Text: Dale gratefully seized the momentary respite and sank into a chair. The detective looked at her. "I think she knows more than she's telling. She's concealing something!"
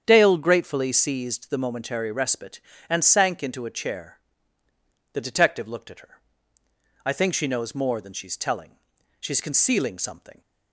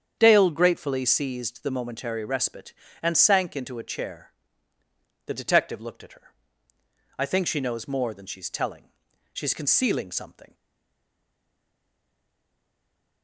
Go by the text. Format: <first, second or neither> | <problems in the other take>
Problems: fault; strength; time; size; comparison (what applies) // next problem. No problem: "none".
first | starts louder than the rest; strong; until 1.2 s; 8 dB; strong in the first // stays silent after the last word; strong; from 10.5 s on; 2.7 s long